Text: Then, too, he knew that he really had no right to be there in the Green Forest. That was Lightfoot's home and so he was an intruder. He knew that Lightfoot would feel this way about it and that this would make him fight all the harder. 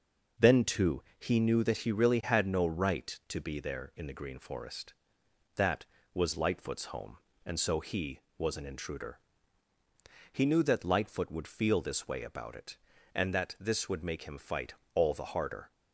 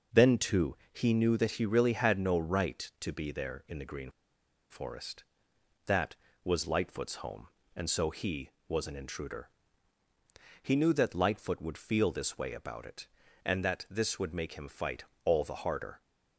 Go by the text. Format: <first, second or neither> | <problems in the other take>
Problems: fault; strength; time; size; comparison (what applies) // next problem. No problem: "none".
first | pauses between "Green" and "Forest"; noticeable; at 4.1 s; 0.59 s long // pauses between "fight" and "all"; slight; at 15.0 s; 0.18 s long; slight in the first